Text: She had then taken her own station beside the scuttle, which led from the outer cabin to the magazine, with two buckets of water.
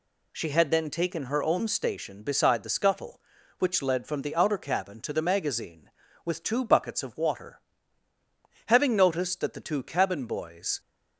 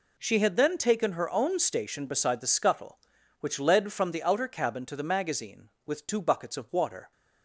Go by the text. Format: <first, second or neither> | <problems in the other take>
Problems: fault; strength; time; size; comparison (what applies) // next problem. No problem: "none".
second | goes on to say "Having noticed that the two cabin boys"; strong; from 8.6 s on; 2.1 s long